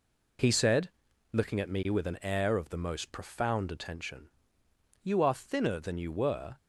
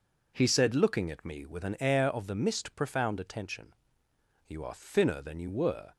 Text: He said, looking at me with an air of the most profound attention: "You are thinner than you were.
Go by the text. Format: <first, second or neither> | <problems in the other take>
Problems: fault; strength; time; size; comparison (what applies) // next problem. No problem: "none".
first | says "mist" for "most"; at 2.3 s